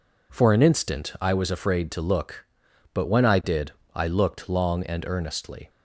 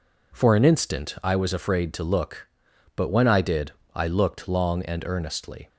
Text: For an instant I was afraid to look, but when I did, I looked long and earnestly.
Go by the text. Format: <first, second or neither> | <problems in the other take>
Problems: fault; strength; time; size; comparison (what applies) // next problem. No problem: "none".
neither | none